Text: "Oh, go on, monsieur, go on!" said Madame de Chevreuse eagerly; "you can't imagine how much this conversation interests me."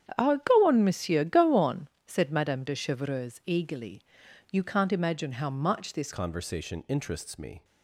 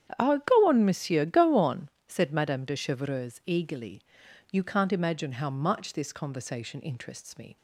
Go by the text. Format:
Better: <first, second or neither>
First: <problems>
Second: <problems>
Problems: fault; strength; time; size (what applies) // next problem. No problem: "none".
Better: second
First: starts louder than the rest; strong; until 1.2 s; 9 dB // changes voice at "conversation"; from 6.1 s on; 1.5 s long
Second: starts louder than the rest; strong; until 1.2 s; 9 dB